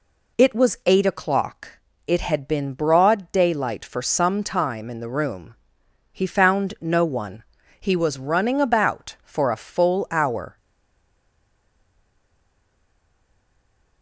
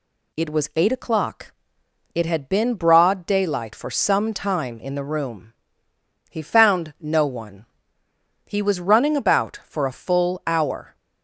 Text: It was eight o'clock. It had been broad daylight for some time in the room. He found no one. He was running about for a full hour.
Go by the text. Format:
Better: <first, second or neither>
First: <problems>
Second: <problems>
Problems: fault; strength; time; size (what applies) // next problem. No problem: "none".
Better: second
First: stays silent after the last word; strong; from 10.5 s on; 3.5 s long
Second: none